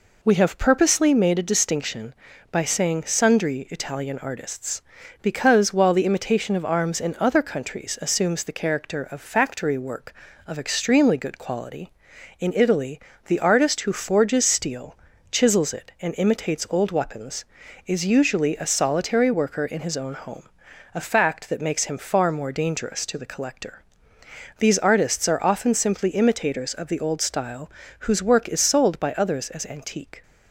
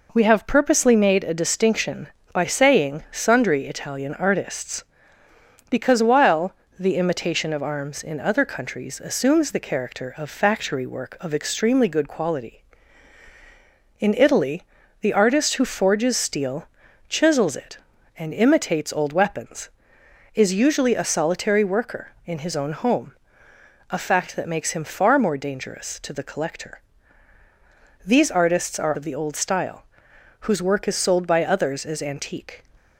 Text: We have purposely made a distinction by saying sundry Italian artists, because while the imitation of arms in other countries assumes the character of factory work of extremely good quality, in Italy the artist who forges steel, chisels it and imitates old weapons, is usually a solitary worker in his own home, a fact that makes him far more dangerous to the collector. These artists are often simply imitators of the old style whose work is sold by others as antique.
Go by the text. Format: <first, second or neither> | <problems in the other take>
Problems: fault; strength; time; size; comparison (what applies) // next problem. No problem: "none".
first | pauses between "while" and "the"; slight; at 6.5 s; 0.24 s long // pauses between "Italy" and "the"; at 14.6 s; 0.38 s long; slight in the first // skips "often simply imitators"; at 28.9 s // pauses between "style" and "whose"; noticeable; at 29.8 s; 0.56 s long; slight in the first